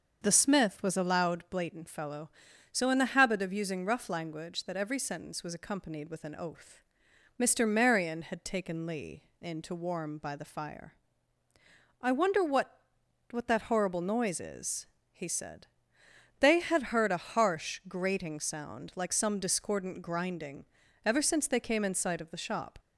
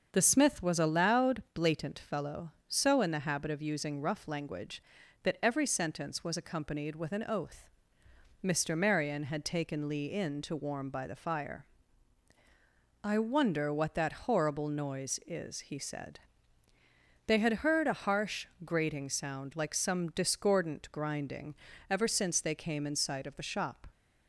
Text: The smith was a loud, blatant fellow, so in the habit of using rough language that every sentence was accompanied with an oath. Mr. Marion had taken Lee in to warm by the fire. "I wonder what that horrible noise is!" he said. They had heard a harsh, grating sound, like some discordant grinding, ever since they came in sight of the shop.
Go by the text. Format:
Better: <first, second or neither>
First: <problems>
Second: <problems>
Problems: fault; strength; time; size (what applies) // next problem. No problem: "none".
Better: second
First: starts louder than the rest; noticeable; until 1.2 s; 6 dB // says "what" twice; at 13.3 s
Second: starts louder than the rest; until 1.1 s; 6.5 dB